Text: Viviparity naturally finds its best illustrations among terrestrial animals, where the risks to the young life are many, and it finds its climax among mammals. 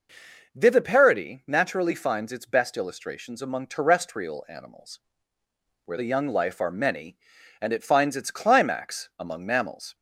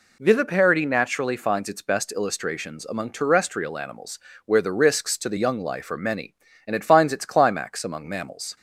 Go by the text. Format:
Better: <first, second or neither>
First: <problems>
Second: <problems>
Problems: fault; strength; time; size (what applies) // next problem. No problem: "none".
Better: second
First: skips "the risks to"; at 5.9 s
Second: none